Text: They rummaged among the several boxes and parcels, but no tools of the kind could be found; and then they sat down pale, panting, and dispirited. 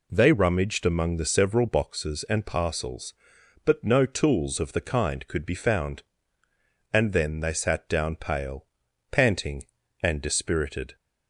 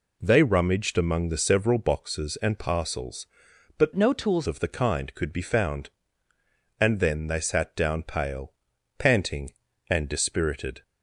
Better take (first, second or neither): first